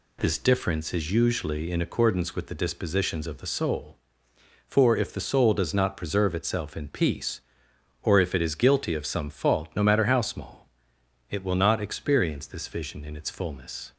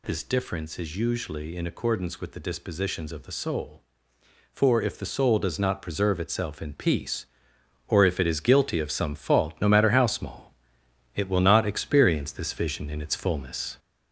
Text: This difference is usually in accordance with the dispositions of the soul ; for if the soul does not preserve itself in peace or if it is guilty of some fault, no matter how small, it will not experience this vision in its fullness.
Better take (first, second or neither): first